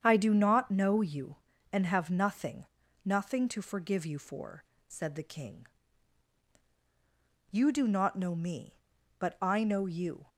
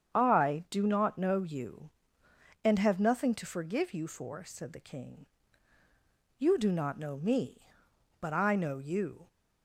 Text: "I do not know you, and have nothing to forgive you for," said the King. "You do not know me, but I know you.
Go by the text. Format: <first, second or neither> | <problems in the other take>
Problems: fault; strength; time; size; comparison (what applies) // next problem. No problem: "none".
second | starts louder than the rest; strong; until 1.0 s; 8 dB; strong in the second // says "nothing" twice; at 3.0 s